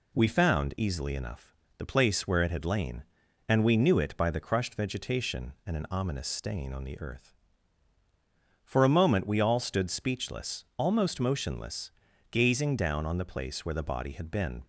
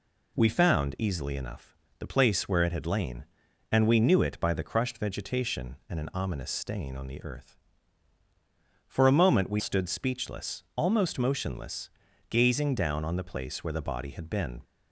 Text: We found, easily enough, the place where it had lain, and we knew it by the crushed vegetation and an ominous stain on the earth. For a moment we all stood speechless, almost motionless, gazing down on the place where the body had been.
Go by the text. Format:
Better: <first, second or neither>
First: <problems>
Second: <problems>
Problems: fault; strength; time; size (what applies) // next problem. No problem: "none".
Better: first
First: none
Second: skips "all"; at 9.5 s